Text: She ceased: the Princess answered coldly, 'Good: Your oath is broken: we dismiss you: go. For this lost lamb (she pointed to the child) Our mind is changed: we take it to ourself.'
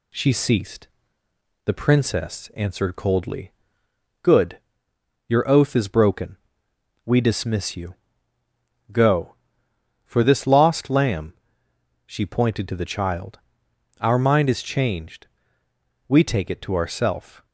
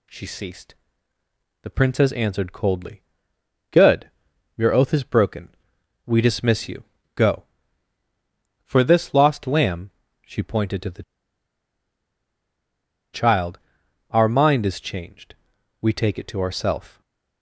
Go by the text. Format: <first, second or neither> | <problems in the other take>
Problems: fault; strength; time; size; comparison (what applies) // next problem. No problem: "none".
first | pauses between "the" and "child"; strong; at 11.0 s; 2.1 s long // stays silent after the last word; slight; from 16.8 s on; 0.6 s long